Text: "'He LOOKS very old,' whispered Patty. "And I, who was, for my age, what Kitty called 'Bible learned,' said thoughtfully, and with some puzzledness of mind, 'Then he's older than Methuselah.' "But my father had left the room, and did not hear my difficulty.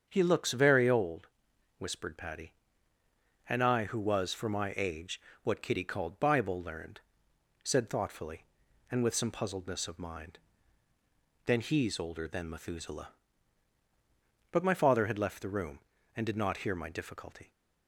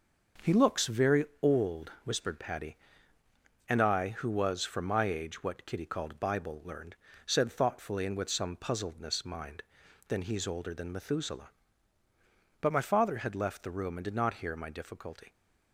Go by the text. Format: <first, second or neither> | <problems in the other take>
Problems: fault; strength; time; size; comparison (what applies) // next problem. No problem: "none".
first | starts louder than the rest; until 1.6 s; 6.5 dB; strong in the first // pauses between "very" and "old"; slight; at 1.2 s; 0.18 s long // skips "of"; at 9.2 s